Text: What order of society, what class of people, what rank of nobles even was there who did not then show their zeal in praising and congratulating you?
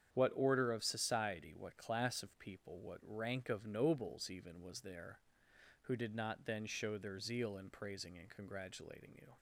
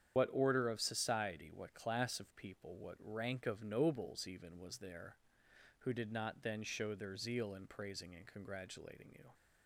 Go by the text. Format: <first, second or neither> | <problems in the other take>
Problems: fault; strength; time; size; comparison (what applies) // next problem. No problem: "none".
first | loses the start of "What"; at 0.1 s; 60 ms // starts louder than the rest; strong; until 1.1 s; 8.5 dB; strong in the first